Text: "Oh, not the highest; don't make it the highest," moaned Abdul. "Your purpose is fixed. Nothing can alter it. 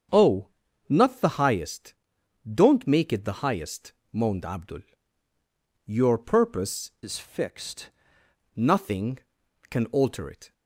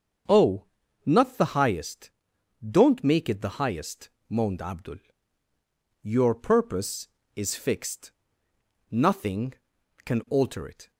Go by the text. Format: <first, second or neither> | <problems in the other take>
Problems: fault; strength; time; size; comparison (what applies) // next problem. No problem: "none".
second | starts louder than the rest; strong; until 1.5 s; 7 dB; also in the second // changes voice from "is" to "fixed"; from 7.0 to 7.9 s; 0.9 s long